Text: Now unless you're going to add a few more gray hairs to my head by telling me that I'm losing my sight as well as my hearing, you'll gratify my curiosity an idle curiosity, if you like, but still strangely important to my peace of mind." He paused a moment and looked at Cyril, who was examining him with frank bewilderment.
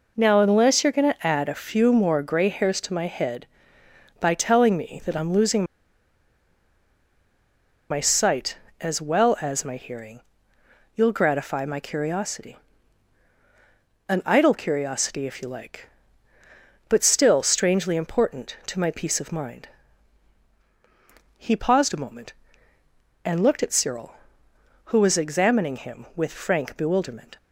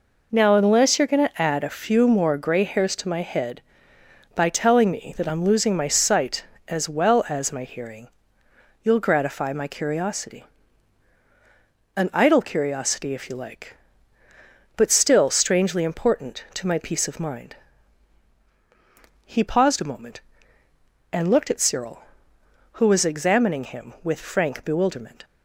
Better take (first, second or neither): second